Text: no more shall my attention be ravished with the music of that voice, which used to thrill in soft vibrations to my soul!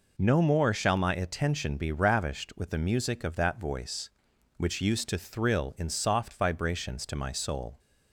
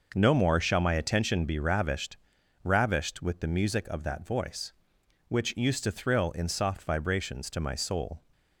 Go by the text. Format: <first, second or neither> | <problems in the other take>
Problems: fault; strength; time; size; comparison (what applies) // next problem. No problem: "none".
first | says "ravished" twice; at 2.6 s